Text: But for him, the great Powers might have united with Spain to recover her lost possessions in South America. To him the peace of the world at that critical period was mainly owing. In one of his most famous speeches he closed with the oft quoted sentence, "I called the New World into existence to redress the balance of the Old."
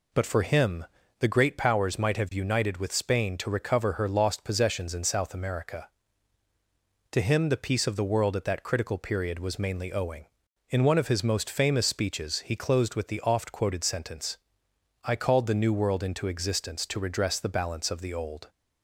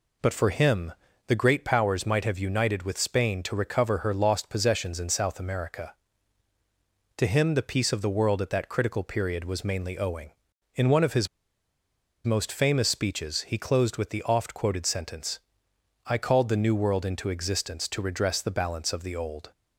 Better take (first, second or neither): first